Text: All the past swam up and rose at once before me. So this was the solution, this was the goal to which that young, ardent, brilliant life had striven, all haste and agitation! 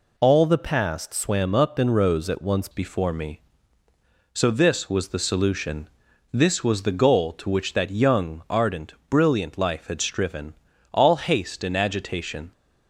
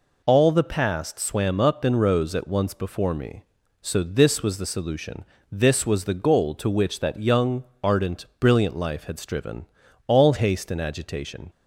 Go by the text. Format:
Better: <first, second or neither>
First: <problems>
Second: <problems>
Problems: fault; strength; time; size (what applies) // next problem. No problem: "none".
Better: second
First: changes voice at "before"; from 2.7 s on; 9.8 s long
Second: none